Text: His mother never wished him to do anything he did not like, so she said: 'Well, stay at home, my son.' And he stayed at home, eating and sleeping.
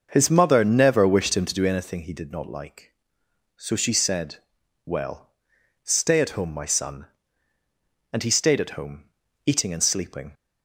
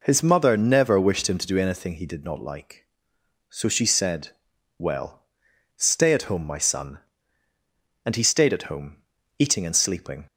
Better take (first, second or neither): second